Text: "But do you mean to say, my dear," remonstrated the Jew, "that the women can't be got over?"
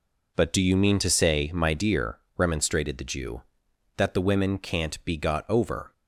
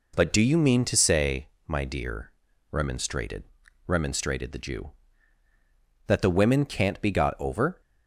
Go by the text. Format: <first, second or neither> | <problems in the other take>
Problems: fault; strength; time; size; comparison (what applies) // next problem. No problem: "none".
first | says "remonstrated" twice; at 3.8 s